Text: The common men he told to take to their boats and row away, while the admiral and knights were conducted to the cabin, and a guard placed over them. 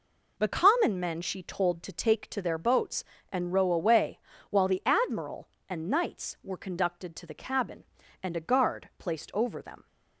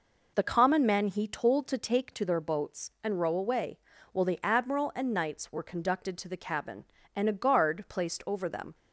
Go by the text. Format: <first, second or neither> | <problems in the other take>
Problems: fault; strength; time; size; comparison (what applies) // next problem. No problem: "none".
second | says "she" for "he"; at 1.2 s